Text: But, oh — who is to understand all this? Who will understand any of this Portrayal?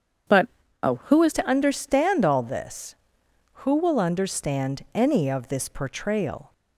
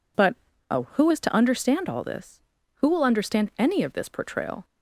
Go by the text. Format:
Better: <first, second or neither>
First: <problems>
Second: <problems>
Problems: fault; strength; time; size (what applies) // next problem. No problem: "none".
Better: second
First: starts louder than the rest; strong; until 1.6 s; 7.5 dB // changes voice at "to"; from 1.3 s on; 5.2 s long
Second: none